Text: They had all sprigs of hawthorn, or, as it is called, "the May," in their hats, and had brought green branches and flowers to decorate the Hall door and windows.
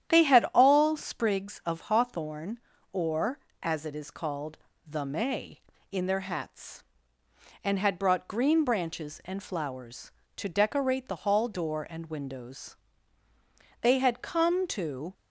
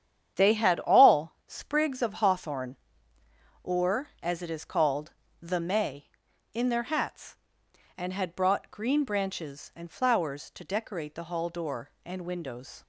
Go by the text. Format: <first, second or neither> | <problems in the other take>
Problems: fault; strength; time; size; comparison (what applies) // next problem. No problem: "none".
second | starts louder than the rest; strong; until 1.1 s; 10.5 dB; strong in the second // goes on to say "They had come to"; from 13.8 s on; 1.3 s long